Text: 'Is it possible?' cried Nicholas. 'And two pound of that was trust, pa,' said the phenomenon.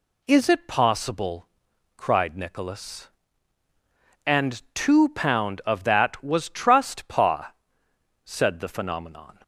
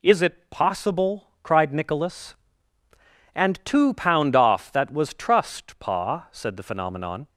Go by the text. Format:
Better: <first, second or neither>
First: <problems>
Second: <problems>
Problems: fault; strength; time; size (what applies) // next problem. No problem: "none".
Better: first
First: none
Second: says "off" for "of"; at 4.3 s